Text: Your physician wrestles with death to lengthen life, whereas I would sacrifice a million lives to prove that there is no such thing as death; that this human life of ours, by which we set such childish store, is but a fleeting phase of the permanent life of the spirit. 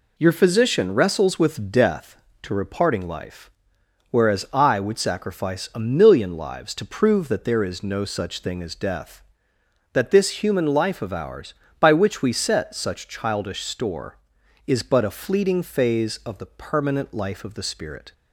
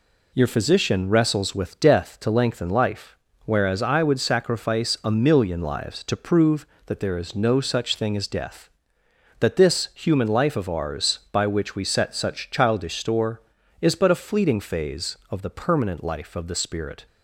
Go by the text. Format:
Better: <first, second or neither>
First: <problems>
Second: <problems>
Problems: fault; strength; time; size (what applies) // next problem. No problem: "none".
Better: second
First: says "reparting" for "lengthen"; at 2.5 s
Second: none